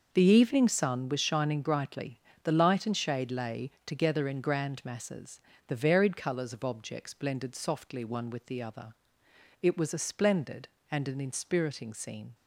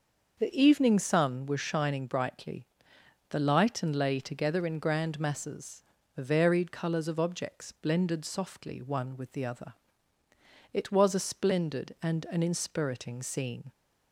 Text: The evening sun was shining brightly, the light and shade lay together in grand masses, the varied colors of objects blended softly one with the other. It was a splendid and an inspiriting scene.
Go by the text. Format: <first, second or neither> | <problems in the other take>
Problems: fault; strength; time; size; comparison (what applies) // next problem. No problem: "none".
first | starts louder than the rest; until 1.4 s; 6 dB; noticeable in the first // skips "shade"; at 3.9 s